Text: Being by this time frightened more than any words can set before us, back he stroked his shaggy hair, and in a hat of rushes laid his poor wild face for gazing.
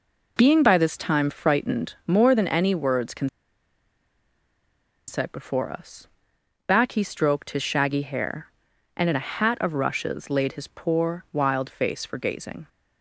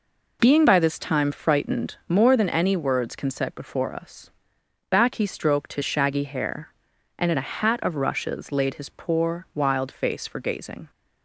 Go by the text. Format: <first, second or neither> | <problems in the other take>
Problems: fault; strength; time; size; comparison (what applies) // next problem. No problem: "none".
second | pauses between "can" and "set"; strong; at 3.2 s; 1.8 s long